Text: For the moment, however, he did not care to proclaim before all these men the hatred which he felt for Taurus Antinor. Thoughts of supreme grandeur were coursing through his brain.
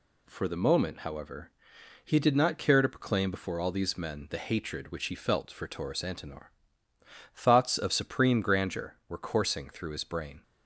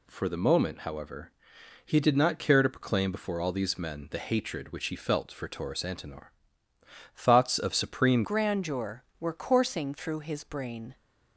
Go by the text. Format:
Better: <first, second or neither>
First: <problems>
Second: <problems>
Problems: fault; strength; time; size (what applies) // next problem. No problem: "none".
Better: first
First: none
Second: changes voice at "grandeur"; from 8.2 s on; 2.7 s long